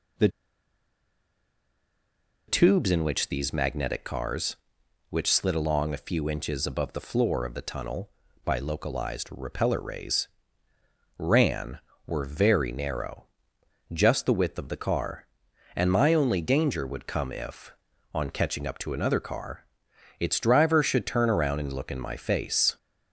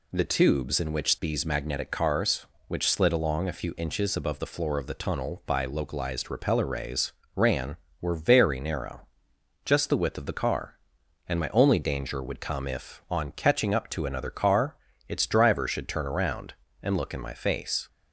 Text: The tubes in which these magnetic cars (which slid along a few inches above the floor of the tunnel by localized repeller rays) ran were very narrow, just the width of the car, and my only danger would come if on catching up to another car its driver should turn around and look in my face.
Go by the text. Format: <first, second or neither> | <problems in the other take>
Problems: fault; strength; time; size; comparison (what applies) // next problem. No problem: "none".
second | pauses between "The" and "tubes"; strong; at 0.2 s; 2.1 s long // pauses between "car" and "its"; noticeable; at 19.6 s; 0.52 s long; slight in the second